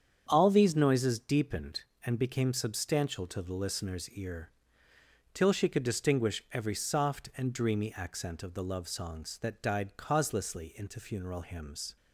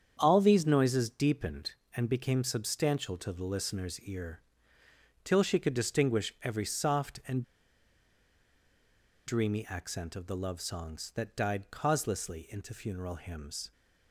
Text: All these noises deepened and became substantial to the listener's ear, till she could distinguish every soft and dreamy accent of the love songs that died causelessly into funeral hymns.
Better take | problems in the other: first | starts louder than the rest; strong; until 1.1 s; 8 dB; strong in the first // pauses between "and" and "dreamy"; strong; at 7.4 s; 1.8 s long

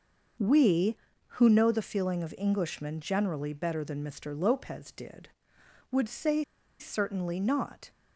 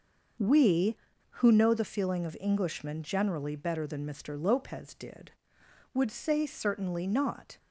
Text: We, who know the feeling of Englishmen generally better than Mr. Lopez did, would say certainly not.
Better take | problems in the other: second | pauses between "say" and "certainly"; at 6.4 s; 0.36 s long

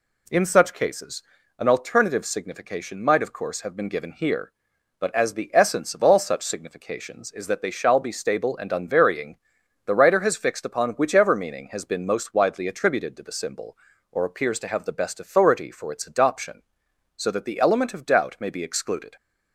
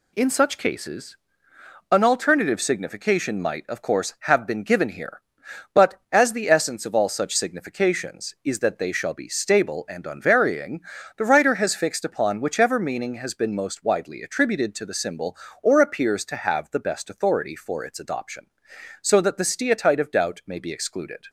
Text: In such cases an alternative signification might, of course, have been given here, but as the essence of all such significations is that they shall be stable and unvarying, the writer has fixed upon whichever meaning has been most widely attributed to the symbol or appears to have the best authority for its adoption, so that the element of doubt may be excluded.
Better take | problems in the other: first | pauses between "cases" and "an"; noticeable; at 1.1 s; 0.74 s long; slight in the first // says "steatite" for "element"; at 19.4 s

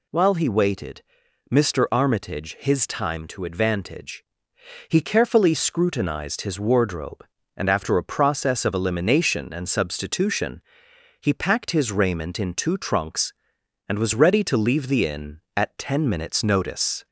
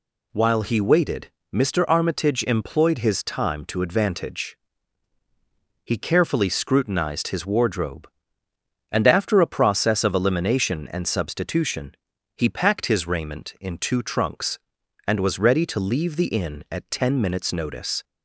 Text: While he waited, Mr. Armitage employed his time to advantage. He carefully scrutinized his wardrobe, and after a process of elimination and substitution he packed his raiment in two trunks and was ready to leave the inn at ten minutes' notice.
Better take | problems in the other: second | skips "employed"; at 2.5 s // pauses between "substitution" and "he"; noticeable; at 10.6 s; 0.60 s long; also in the second

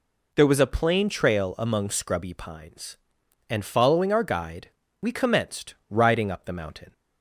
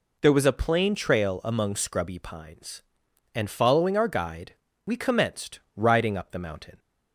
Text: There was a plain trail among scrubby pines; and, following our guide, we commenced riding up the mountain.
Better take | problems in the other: neither | pauses between "commenced" and "riding"; slight; the same in both

